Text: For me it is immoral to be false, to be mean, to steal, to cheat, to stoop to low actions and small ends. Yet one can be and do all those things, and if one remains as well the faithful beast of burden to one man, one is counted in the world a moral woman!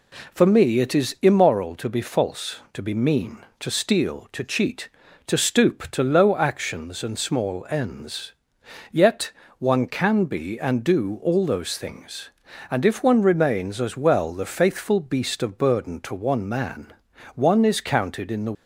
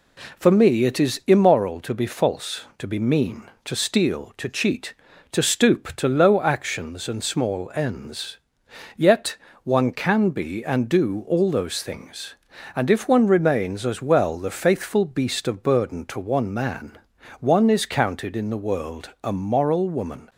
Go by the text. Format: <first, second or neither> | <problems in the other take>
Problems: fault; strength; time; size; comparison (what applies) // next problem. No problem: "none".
second | pauses between "Yet" and "one"; slight; at 9.3 s; 0.26 s long; slight in the second // stops before "world a moral woman"; at 18.5 s